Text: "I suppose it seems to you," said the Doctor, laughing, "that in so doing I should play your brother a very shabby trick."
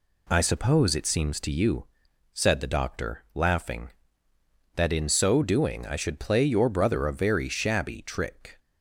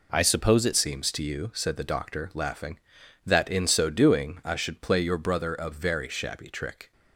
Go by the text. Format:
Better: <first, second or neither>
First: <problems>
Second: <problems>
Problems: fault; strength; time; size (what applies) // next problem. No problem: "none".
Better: first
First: none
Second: changes voice at "seems"; from 0.7 s on; 6.2 s long